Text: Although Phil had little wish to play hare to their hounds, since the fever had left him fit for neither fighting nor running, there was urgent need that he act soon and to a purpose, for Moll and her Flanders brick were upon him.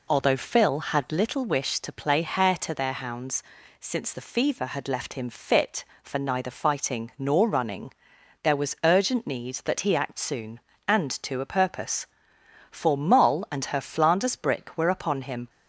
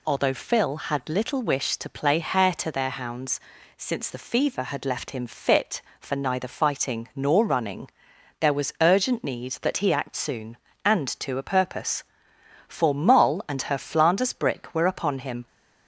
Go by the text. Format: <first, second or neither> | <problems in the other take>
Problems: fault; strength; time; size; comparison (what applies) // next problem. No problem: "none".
second | starts louder than the rest; slight; until 1.3 s; 3 dB